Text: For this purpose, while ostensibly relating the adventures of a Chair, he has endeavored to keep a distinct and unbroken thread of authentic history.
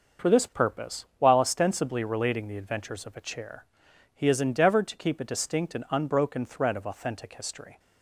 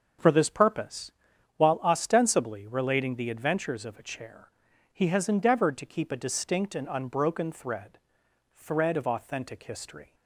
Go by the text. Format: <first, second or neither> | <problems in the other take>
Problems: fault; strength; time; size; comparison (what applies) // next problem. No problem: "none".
first | starts louder than the rest; until 1.6 s; 6.5 dB; also in the first // says "thread" twice; at 8.5 s